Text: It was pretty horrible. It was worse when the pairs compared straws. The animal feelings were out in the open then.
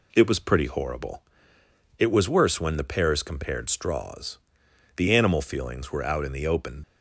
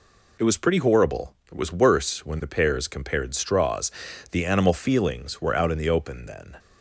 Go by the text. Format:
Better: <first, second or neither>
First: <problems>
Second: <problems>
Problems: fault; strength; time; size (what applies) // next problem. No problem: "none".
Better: second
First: stops before "then"; at 6.8 s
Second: none